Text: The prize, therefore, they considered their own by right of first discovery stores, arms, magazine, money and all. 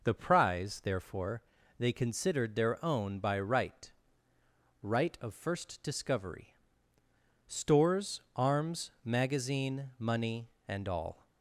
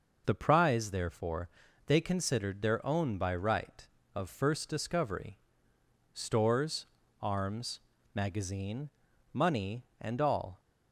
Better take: second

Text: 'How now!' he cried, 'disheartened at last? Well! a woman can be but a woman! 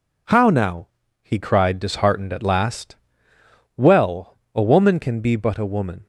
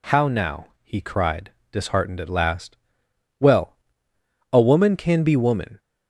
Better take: first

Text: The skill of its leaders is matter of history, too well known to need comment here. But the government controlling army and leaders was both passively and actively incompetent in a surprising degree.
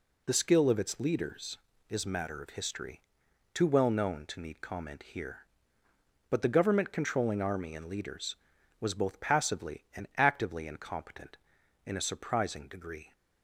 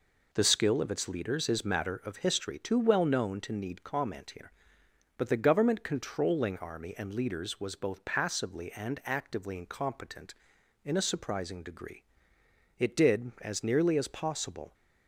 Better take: first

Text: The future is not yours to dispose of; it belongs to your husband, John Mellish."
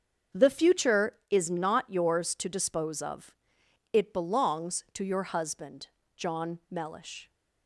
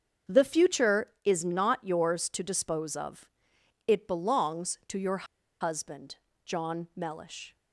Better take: first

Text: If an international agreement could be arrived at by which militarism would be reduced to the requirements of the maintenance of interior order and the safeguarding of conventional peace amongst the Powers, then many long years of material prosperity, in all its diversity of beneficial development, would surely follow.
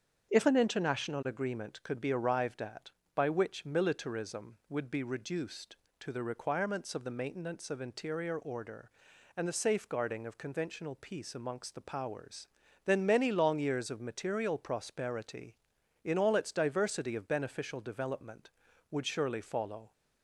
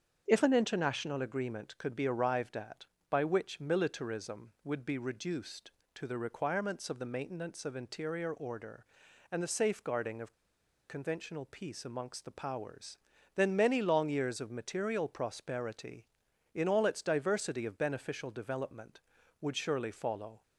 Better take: first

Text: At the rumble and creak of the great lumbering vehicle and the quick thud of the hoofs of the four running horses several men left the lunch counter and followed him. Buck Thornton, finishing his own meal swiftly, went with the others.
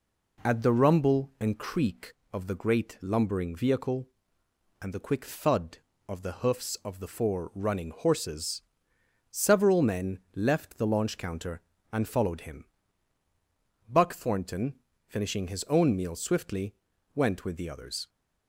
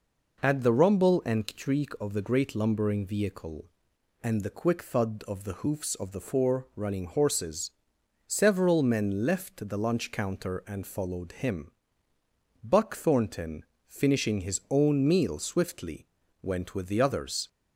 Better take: second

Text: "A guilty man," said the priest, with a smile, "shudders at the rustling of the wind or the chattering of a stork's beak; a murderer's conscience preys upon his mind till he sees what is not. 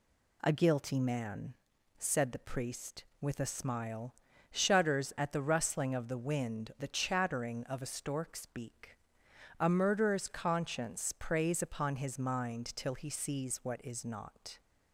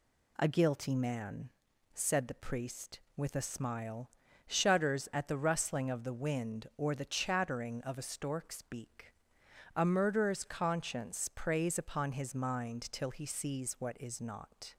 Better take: second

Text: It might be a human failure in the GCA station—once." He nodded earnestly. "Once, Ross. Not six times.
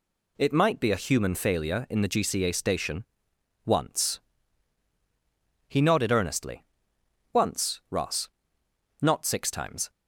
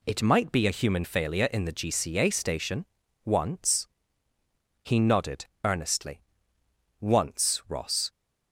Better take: first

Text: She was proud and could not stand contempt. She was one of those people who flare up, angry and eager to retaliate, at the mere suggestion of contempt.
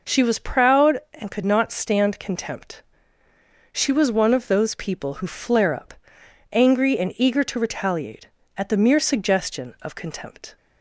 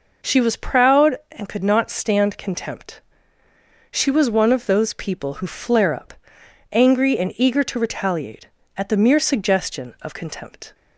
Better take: neither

